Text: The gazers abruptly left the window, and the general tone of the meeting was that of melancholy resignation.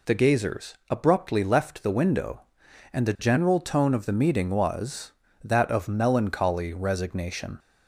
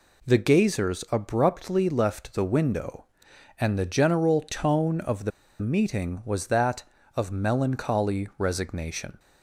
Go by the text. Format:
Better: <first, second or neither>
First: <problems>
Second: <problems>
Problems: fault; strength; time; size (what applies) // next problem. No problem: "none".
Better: first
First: none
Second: pauses between "the" and "meeting"; slight; at 5.3 s; 0.30 s long